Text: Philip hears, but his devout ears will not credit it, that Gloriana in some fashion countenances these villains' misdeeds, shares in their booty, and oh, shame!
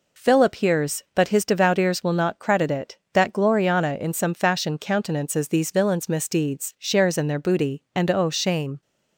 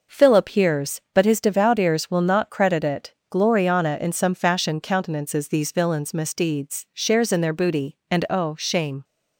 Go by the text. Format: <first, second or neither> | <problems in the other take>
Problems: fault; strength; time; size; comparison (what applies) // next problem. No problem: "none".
first | skips "that"; at 3.2 s